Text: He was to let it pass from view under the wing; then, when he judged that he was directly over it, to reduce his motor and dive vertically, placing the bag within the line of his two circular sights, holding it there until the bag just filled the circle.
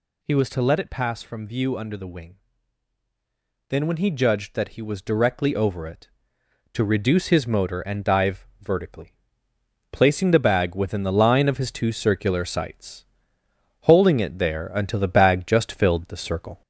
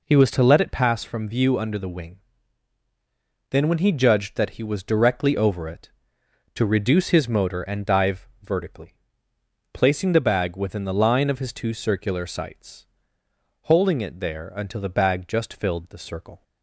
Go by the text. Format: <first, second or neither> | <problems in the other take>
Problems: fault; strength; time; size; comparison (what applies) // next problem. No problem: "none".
second | gets louder; slight; throughout; 3 dB